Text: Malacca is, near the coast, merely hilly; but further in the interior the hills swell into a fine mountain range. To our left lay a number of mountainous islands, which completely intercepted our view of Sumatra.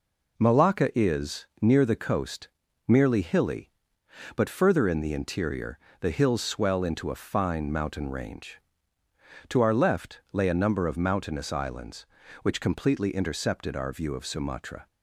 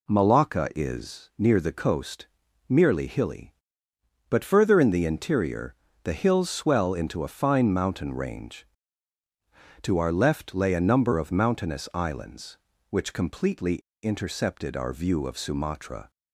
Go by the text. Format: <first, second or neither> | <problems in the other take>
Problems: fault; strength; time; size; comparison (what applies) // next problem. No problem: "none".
first | pauses between "interior" and "the"; slight; at 5.7 s; 0.30 s long; slight in the first // pauses between "completely" and "intercepted"; slight; at 13.7 s; 0.27 s long